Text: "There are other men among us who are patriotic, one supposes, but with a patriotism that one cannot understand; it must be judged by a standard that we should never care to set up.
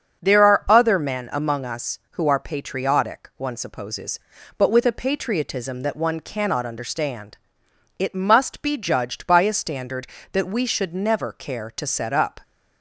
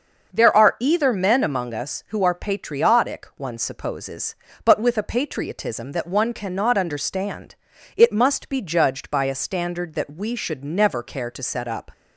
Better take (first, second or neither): first